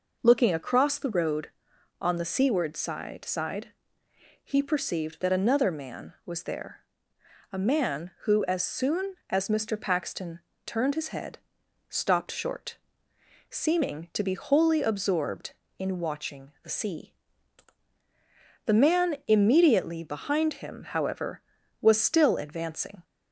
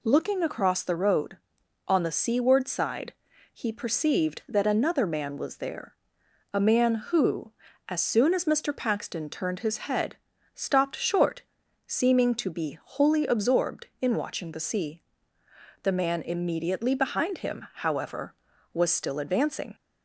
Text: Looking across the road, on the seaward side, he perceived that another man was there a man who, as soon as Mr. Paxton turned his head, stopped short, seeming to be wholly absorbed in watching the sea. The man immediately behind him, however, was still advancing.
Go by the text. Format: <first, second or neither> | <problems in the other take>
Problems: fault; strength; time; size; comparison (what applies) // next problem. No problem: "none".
second | says "side" twice; at 3.2 s // pauses between "there" and "a"; noticeable; at 6.7 s; 0.72 s long; noticeable in the second // pauses between "Paxton" and "turned"; slight; at 10.3 s; 0.26 s long